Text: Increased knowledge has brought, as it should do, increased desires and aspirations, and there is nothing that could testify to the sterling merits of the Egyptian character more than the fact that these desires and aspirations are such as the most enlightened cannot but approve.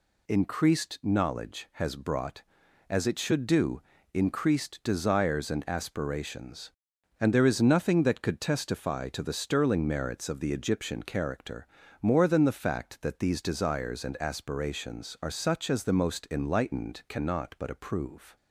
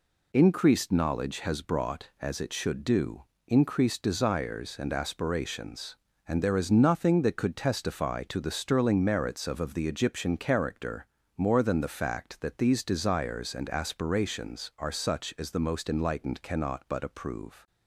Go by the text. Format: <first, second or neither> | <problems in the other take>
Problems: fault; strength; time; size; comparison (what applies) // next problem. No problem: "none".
first | says "of" twice; at 9.5 s // pauses between "character" and "more"; slight; at 11.0 s; 0.32 s long; slight in the first